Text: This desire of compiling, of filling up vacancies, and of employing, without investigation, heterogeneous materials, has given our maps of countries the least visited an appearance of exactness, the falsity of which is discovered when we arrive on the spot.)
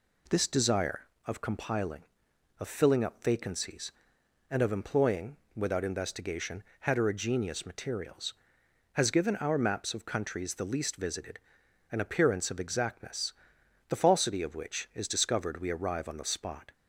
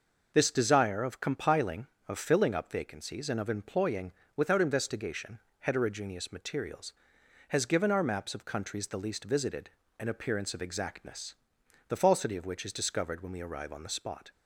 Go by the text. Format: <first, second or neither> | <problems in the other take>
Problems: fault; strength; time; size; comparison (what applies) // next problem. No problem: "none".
second | pauses between "visited" and "an"; noticeable; at 11.3 s; 0.54 s long; slight in the second // skips "when"; at 15.6 s